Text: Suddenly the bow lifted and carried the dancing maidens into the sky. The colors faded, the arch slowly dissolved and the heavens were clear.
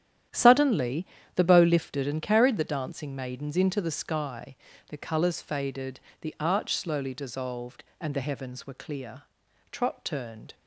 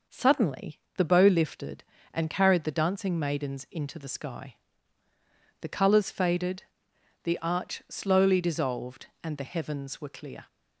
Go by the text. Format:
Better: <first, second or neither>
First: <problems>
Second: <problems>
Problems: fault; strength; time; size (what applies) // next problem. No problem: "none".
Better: second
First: starts louder than the rest; strong; until 1.6 s; 10.5 dB // pauses between "Suddenly" and "the"; slight; at 1.0 s; 0.30 s long // goes on to say "Trot turned"; noticeable; from 9.7 s on; 0.84 s long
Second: pauses between "Suddenly" and "the"; slight; at 0.7 s; 0.18 s long